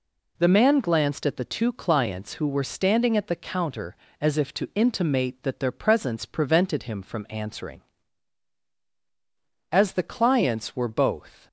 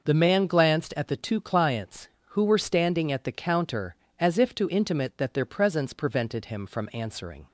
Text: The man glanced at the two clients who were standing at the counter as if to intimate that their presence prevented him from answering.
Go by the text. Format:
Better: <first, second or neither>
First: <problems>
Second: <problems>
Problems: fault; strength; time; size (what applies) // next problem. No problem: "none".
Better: second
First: goes on to say "As the clients were both"; strong; from 9.7 s on; 1.7 s long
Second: none